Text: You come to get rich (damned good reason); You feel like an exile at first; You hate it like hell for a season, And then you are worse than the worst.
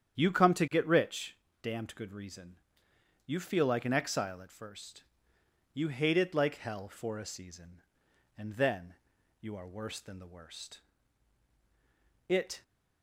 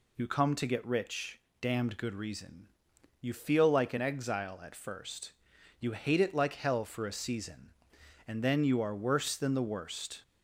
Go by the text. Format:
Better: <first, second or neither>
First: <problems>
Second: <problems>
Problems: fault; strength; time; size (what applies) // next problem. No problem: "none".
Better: second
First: starts louder than the rest; strong; until 1.2 s; 9 dB // pauses between "then" and "you"; noticeable; at 8.9 s; 0.46 s long // goes on to say "It"; slight; from 12.2 s on; 0.36 s long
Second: none